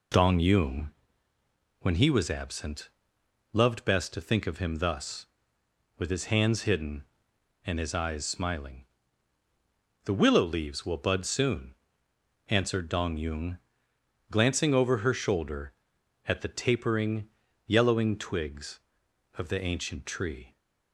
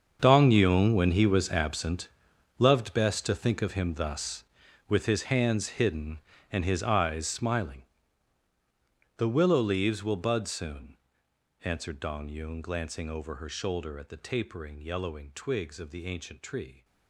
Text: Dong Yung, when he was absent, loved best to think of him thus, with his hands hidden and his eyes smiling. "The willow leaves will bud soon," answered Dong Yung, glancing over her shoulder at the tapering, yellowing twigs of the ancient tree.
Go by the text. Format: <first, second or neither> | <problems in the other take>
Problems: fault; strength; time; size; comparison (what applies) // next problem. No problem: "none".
first | gets quieter; strong; throughout; 16 dB